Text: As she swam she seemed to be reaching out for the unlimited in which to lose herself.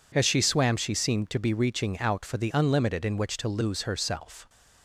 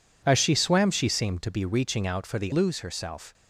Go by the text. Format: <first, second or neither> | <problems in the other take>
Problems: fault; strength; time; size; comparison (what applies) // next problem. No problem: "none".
first | skips "unlimited in which to"; at 2.5 s